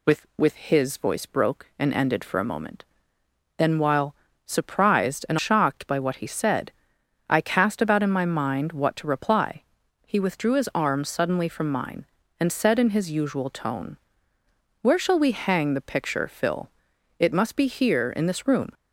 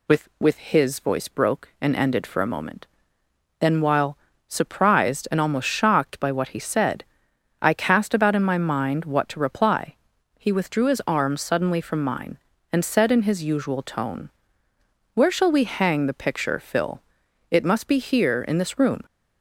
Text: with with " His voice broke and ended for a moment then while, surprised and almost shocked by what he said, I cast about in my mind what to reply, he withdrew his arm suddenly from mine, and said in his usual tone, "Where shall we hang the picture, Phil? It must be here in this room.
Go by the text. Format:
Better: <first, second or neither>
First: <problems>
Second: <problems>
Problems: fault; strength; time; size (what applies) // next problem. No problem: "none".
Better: second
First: pauses between "moment" and "then"; noticeable; at 2.8 s; 0.72 s long // skips "almost"; at 5.3 s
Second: pauses between "moment" and "then"; noticeable; at 2.8 s; 0.72 s long